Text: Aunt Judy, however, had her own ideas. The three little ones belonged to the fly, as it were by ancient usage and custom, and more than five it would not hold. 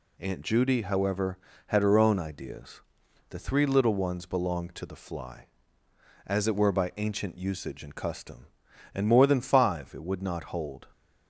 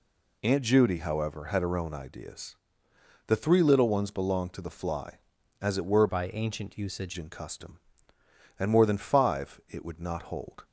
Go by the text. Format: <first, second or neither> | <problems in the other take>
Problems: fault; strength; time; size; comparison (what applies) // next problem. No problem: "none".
first | changes voice from "by" to "usage"; from 6.0 to 7.1 s; 1.1 s long